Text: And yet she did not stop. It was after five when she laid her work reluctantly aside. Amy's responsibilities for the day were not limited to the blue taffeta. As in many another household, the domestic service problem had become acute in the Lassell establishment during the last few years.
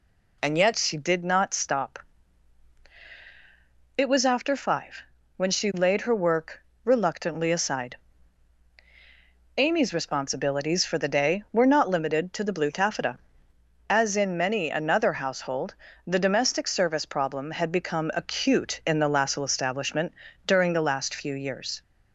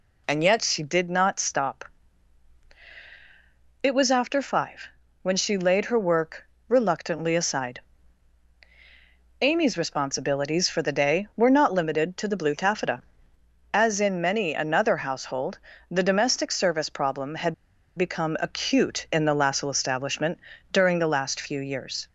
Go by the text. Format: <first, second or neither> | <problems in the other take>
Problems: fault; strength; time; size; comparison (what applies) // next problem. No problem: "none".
first | pauses between "five" and "when"; slight; at 4.8 s; 0.34 s long; slight in the first // pauses between "work" and "reluctantly"; slight; at 6.4 s; 0.20 s long; slight in the first // pauses between "had" and "become"; at 17.5 s; 0.42 s long // pauses between "establishment" and "during"; slight; at 20.3 s; 0.32 s long; slight in the first